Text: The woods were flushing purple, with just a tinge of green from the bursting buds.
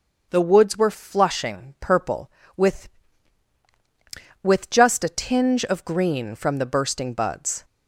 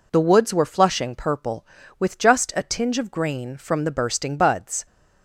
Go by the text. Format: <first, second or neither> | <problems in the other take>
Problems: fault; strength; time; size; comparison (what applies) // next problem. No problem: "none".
second | starts louder than the rest; until 1.3 s; 6.5 dB // says "with" twice; at 4.4 s